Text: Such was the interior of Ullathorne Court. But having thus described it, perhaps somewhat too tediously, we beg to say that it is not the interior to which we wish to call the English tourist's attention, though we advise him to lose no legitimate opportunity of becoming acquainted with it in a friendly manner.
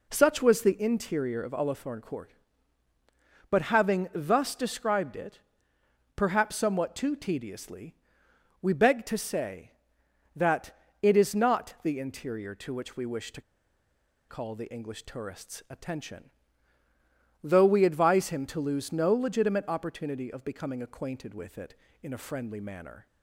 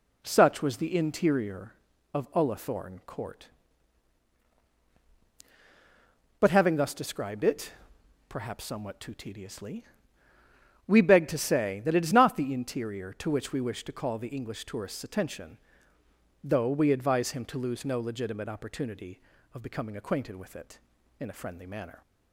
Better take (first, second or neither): second